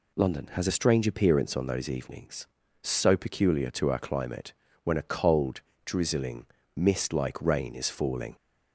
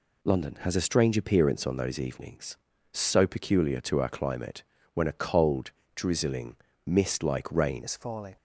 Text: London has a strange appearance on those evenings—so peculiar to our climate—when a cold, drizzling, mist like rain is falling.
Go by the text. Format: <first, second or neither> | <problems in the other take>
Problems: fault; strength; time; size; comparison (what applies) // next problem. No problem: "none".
first | changes voice at "is"; from 7.8 s on; 0.5 s long